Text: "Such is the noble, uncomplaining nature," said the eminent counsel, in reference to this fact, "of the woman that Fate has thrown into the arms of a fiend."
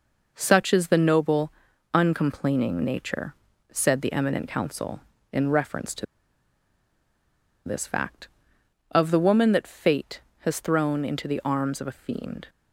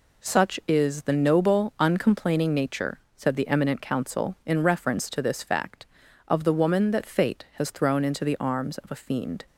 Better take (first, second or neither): second